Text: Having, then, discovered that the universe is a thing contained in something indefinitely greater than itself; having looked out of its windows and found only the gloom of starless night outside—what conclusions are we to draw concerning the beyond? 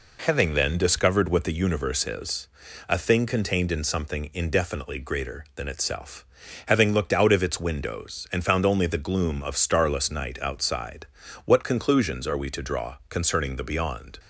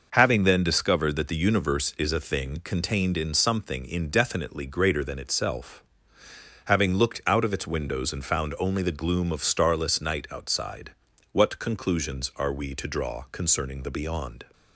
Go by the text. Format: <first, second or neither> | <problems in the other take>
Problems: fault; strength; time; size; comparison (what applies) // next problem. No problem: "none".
second | says "what" for "that"; at 1.3 s // pauses between "is" and "a"; at 2.4 s; 0.44 s long